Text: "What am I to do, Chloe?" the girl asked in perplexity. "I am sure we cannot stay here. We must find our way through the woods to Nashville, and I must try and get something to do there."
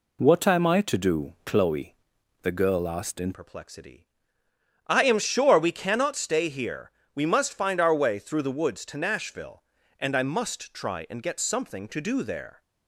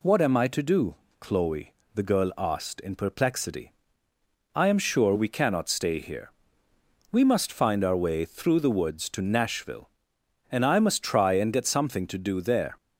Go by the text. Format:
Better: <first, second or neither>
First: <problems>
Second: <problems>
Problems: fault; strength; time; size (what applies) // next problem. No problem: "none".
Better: second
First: changes voice at "perplexity"; from 3.3 s on; 9.3 s long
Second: none